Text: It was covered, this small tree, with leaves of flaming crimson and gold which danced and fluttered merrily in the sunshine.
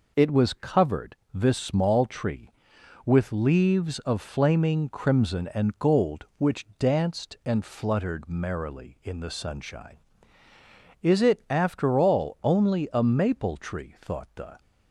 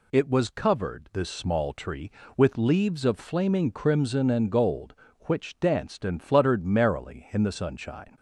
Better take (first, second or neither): second